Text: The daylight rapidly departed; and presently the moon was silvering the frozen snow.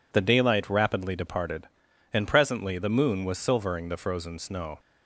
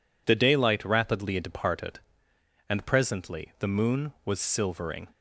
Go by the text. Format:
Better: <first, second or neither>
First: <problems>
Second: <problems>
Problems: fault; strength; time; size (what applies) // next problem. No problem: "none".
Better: first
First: none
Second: stops before "the frozen snow"; at 5.1 s